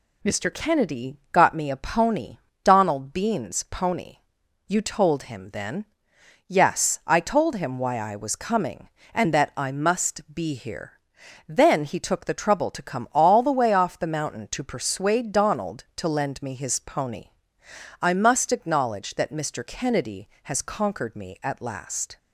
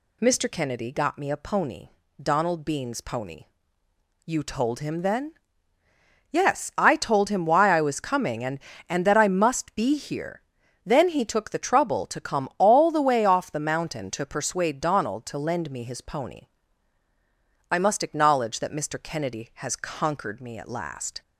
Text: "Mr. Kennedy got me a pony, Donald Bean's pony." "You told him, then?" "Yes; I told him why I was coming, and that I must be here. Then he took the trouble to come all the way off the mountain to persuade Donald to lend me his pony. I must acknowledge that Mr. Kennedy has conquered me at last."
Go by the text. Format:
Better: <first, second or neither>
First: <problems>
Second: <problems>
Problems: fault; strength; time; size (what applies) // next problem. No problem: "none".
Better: first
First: none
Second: says "and" twice; at 8.8 s